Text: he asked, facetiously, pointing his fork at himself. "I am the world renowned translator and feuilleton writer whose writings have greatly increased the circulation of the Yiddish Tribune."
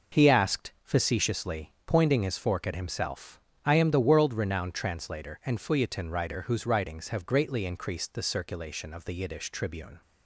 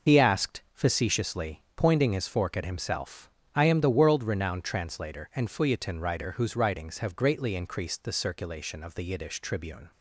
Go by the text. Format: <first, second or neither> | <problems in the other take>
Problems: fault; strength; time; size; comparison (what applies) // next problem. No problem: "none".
first | loses the start of "he"; at 0.0 s; 45 ms